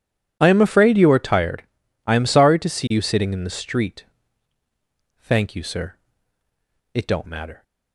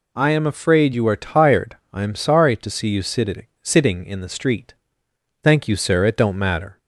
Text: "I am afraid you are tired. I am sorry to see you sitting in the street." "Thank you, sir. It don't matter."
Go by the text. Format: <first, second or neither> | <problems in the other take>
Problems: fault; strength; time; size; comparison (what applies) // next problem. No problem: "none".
first | says "sitting" twice; at 3.6 s